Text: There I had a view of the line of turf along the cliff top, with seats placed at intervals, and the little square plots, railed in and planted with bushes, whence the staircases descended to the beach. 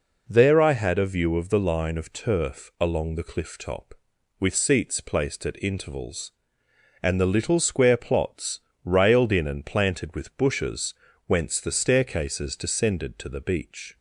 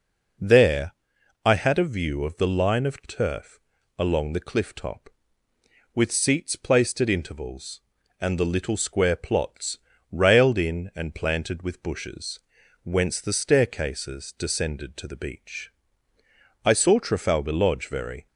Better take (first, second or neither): first